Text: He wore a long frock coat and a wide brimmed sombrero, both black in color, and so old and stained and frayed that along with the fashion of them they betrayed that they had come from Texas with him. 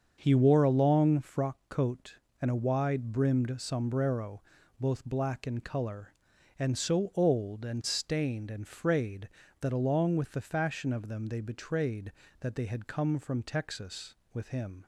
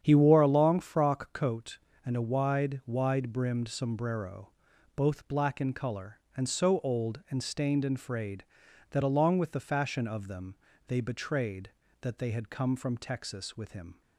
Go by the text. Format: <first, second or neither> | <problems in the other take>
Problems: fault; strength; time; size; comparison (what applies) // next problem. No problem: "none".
first | starts louder than the rest; strong; until 1.0 s; 8.5 dB; also in the first // says "wide" twice; at 2.8 s // pauses between "them" and "they"; slight; at 10.5 s; 0.32 s long